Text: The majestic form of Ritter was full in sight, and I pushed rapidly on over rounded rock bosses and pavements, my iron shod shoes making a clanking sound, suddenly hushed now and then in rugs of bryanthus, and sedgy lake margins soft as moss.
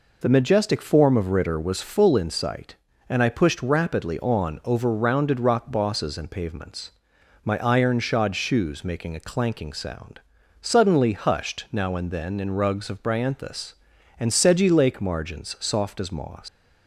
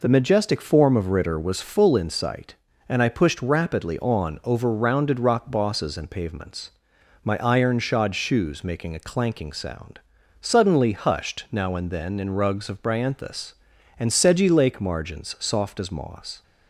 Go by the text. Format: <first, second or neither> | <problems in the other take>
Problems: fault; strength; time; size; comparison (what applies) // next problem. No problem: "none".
second | leaves "moss" unfinished; at 16.4 s; 140 ms